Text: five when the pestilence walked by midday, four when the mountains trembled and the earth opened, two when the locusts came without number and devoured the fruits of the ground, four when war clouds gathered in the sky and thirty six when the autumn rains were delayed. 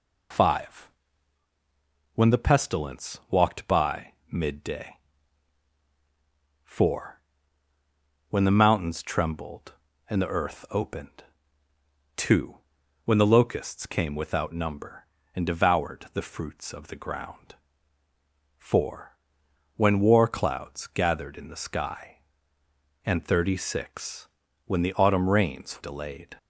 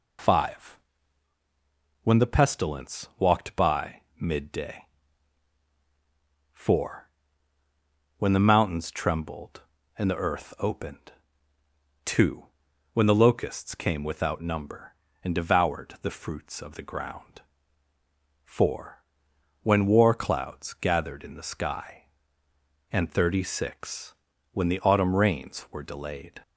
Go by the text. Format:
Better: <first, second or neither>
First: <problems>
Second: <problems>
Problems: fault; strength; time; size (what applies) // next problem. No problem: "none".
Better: second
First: pauses between "five" and "when"; strong; at 0.8 s; 1.2 s long // pauses between "by" and "midday"; slight; at 4.1 s; 0.18 s long // pauses between "four" and "when"; at 7.1 s; 1.1 s long // pauses between "two" and "when"; at 12.5 s; 0.44 s long // pauses between "four" and "when"; noticeable; at 19.1 s; 0.58 s long // pauses between "six" and "when"; slight; at 24.2 s; 0.36 s long // skips "were"; at 25.8 s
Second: pauses between "five" and "when"; strong; at 0.7 s; 1.2 s long // pauses between "by" and "midday"; slight; at 4.0 s; 0.18 s long // pauses between "four" and "when"; at 7.0 s; 1.1 s long // pauses between "two" and "when"; at 12.4 s; 0.44 s long // pauses between "four" and "when"; noticeable; at 19.0 s; 0.58 s long // pauses between "six" and "when"; slight; at 24.1 s; 0.36 s long